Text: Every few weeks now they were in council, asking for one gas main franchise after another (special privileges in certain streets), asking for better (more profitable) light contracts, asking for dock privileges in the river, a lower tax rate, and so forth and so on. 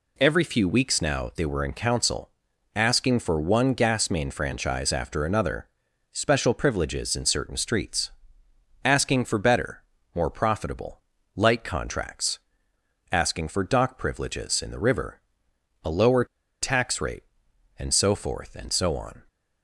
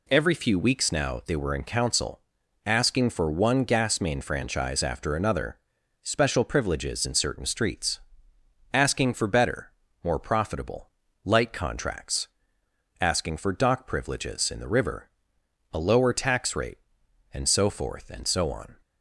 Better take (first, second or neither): second